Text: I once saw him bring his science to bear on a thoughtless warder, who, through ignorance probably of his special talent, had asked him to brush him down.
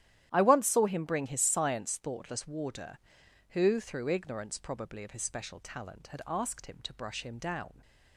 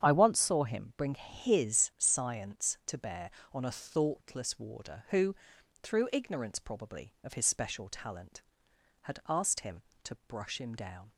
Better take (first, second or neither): second